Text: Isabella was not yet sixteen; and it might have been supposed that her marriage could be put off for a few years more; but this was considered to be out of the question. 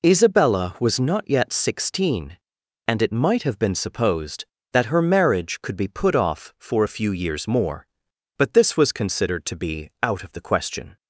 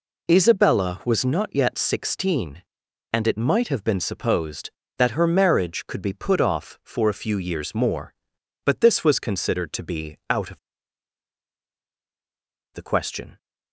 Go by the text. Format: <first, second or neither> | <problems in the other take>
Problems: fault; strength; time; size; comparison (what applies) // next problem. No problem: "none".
first | pauses between "of" and "the"; strong; at 10.5 s; 2.1 s long